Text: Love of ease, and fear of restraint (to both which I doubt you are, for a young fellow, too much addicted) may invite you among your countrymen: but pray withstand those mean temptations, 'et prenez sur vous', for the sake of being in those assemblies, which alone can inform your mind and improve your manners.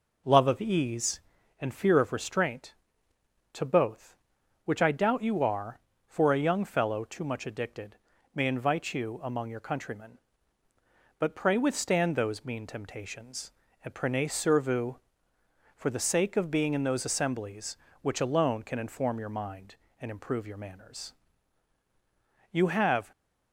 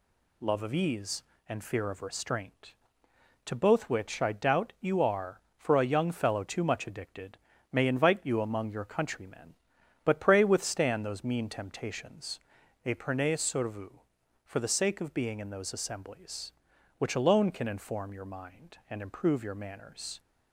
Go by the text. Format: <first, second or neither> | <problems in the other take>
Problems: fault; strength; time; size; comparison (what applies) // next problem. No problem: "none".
second | goes on to say "You have"; from 22.5 s on; 0.60 s long